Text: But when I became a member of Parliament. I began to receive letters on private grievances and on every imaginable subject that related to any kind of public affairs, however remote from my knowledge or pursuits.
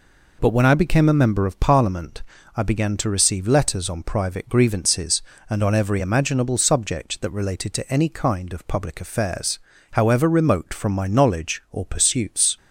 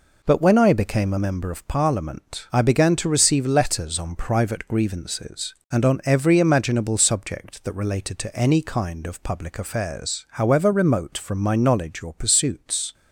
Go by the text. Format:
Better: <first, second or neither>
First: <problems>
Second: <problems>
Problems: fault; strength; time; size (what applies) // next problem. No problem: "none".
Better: neither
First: none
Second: none